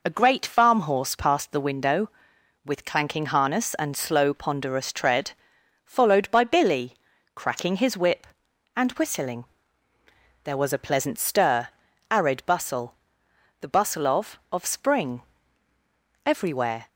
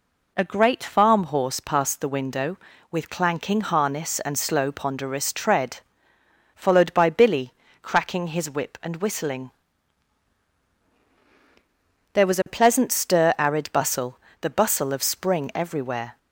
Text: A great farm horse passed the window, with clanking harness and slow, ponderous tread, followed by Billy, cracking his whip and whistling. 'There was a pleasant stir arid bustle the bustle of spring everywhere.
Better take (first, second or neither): second